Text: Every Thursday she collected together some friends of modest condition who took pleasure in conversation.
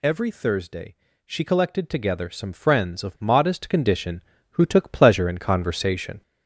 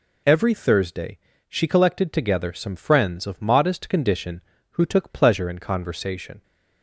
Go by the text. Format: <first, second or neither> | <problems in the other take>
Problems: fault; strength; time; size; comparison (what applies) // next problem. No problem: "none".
second | gets louder; noticeable; throughout; 5 dB // pauses between "Thursday" and "she"; slight; at 0.9 s; 0.30 s long; slight in the second